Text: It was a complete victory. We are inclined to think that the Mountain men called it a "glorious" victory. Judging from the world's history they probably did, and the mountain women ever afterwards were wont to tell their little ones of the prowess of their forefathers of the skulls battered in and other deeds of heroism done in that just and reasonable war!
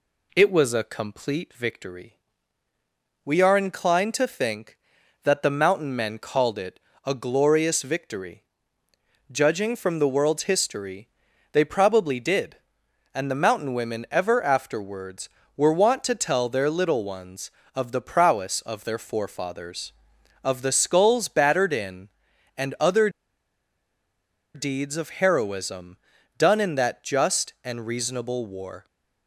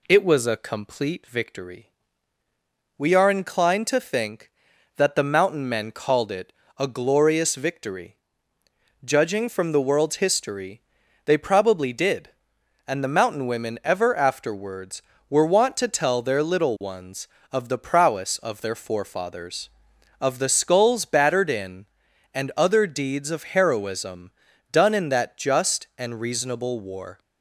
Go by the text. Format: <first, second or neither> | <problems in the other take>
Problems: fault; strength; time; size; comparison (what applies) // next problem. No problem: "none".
second | pauses between "it" and "a"; slight; at 6.7 s; 0.26 s long; slight in the second // pauses between "history" and "they"; at 11.0 s; 0.42 s long; also in the second // pauses between "other" and "deeds"; strong; at 23.0 s; 1.4 s long // pauses between "heroism" and "done"; at 25.9 s; 0.40 s long; also in the second